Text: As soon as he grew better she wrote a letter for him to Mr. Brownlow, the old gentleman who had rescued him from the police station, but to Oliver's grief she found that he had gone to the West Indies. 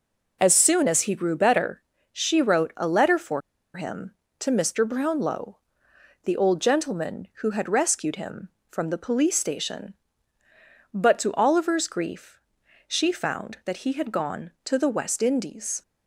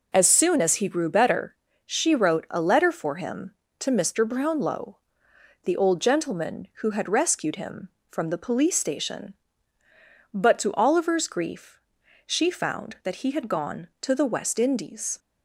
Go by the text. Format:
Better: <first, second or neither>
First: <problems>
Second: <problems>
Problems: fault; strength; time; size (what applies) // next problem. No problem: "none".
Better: second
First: pauses between "better" and "she"; slight; at 1.8 s; 0.30 s long // pauses between "for" and "him"; slight; at 3.4 s; 0.35 s long // pauses between "grief" and "she"; noticeable; at 12.3 s; 0.48 s long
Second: pauses between "better" and "she"; slight; at 1.5 s; 0.30 s long // pauses between "grief" and "she"; noticeable; at 11.7 s; 0.46 s long